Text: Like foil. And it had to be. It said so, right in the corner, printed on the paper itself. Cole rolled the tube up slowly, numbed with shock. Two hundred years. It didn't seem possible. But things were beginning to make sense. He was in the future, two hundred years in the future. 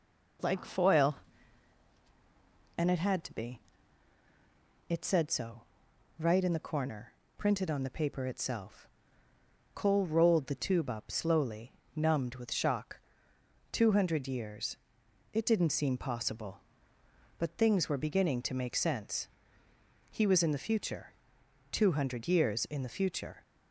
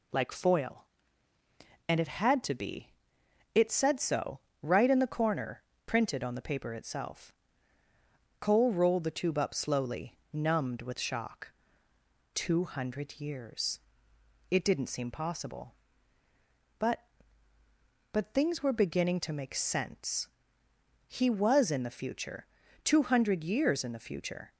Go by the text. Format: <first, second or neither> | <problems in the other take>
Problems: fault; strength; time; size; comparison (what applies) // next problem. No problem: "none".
first | says "But" twice; at 18.1 s